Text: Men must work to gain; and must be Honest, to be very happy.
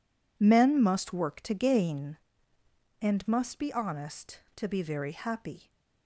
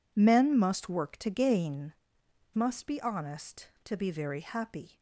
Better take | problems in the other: first | skips "and"; at 2.2 s

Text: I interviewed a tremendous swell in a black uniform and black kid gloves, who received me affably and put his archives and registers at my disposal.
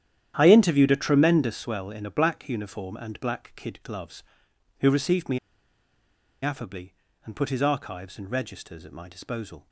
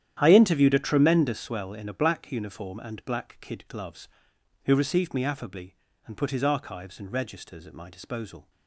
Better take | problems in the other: second | starts louder than the rest; strong; until 1.3 s; 10.5 dB; strong in the second // pauses between "me" and "affably"; at 5.3 s; 1.0 s long

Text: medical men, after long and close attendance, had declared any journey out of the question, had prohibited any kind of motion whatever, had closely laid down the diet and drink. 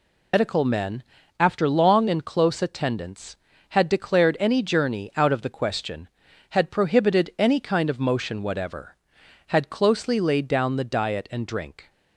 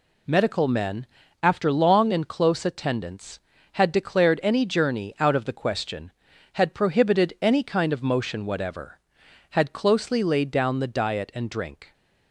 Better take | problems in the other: second | loses the start of "medical"; at 0.3 s; 100 ms

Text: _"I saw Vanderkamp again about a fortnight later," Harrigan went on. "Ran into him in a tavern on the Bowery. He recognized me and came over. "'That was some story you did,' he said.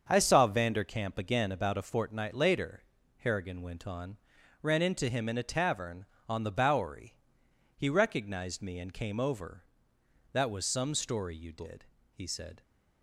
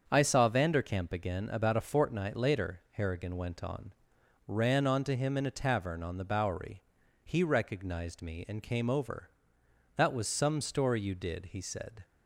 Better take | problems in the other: first | starts louder than the rest; until 1.1 s; 7 dB; also in the first // says "onto" for "into"; at 4.8 s

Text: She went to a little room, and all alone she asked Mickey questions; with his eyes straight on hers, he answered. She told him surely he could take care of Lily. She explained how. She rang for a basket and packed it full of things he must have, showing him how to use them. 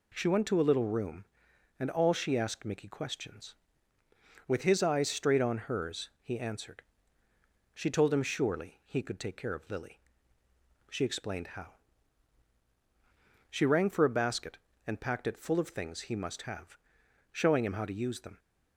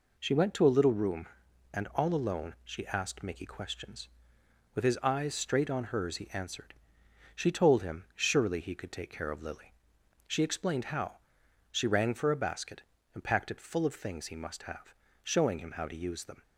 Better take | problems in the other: second | skips "alone"; at 2.1 s

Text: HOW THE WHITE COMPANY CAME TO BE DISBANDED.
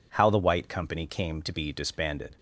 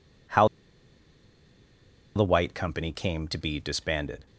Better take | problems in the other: first | pauses between "HOW" and "THE"; strong; at 0.4 s; 1.6 s long

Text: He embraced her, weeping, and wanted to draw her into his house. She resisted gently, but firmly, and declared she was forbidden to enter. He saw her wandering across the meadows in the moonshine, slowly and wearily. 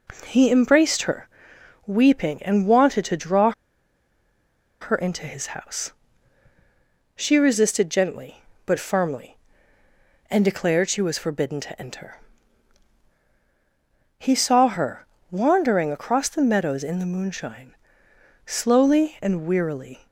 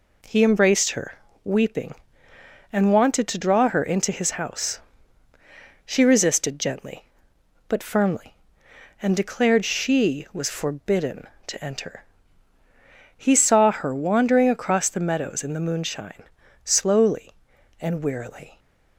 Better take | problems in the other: second | pauses between "draw" and "her"; strong; at 3.5 s; 1.2 s long // pauses between "her" and "wandering"; slight; at 15.0 s; 0.24 s long

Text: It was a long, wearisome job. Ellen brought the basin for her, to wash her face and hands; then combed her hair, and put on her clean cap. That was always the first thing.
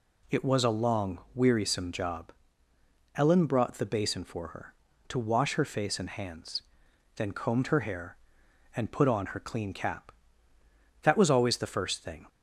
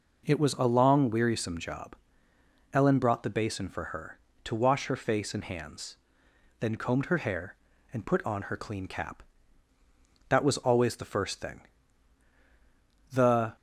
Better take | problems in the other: first | goes on to say "The"; slight; from 13.1 s on; 0.42 s long

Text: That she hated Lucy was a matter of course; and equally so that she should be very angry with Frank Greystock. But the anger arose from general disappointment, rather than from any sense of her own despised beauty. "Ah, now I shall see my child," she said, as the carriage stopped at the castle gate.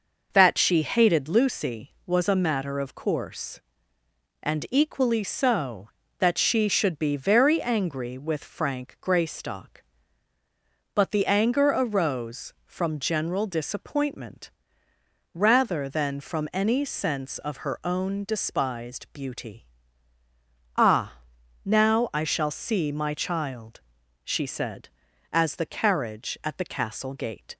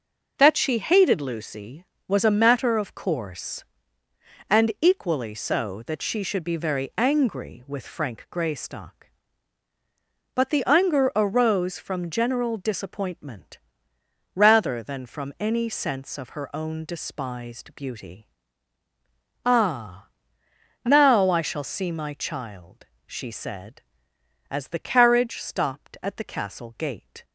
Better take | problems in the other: second | skips "stopped"; at 26.4 s

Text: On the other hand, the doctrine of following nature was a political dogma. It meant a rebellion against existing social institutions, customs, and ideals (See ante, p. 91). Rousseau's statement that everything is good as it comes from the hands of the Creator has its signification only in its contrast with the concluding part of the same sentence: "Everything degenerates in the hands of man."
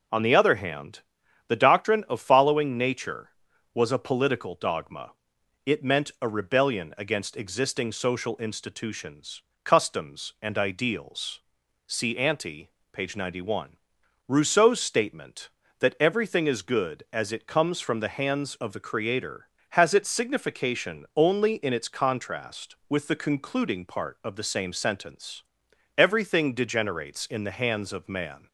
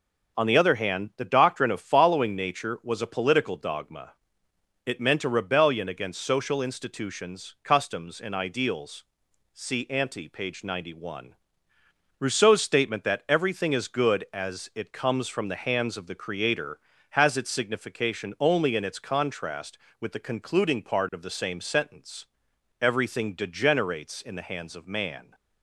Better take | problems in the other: first | skips "existing"; at 6.2 s

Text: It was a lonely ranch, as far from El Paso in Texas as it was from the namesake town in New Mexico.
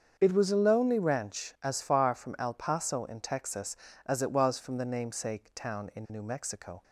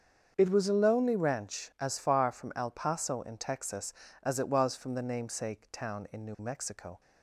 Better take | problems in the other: neither | starts louder than the rest; strong; the same in both

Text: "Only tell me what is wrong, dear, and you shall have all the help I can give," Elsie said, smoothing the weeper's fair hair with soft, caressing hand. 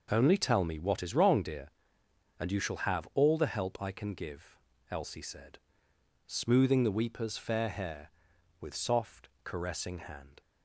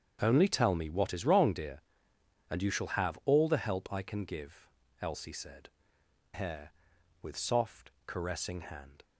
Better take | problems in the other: first | starts louder than the rest; strong; until 1.2 s; 7.5 dB // skips "smoothing the weeper's fair"; at 6.0 s

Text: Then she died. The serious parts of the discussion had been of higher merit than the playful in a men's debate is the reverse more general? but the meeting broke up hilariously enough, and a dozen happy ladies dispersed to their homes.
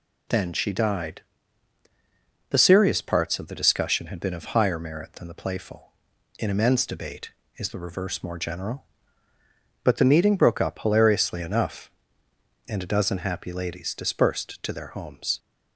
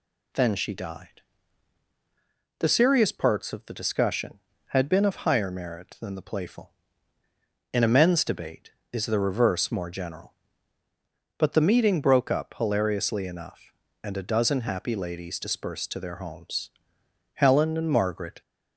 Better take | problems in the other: first | goes on to say "Helen and Margaret"; noticeable; from 17.3 s on; 1.0 s long

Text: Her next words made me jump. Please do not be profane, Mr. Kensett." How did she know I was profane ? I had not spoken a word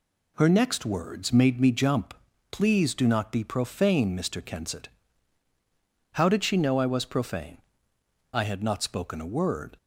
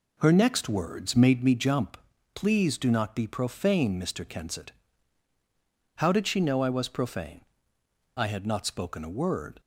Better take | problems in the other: first | starts louder than the rest; slight; until 1.5 s; 3.5 dB

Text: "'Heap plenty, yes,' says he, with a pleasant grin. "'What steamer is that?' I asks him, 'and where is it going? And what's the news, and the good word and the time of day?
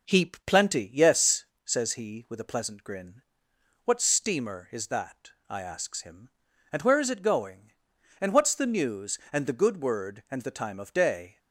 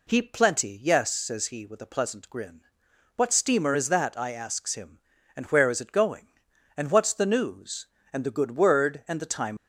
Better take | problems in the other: first | stops before "of day"; at 9.5 s

